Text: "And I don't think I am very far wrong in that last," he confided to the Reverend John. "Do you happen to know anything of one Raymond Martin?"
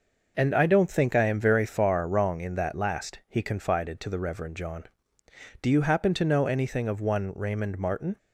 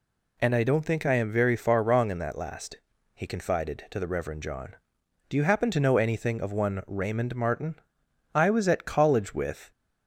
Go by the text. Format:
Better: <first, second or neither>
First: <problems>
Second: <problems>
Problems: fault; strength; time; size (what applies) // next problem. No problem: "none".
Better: first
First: none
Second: goes on to say "I was at College with"; from 8.3 s on; 1.3 s long